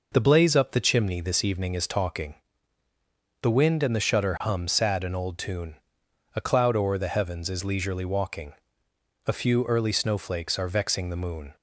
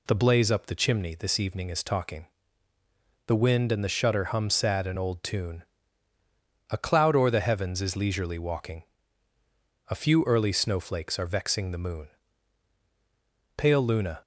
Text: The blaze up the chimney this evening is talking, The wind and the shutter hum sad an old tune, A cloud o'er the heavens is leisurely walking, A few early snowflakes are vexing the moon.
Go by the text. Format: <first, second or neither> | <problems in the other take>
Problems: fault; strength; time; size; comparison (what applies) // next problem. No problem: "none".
first | goes on to say "Pale Luna"; noticeable; from 13.5 s on; 0.64 s long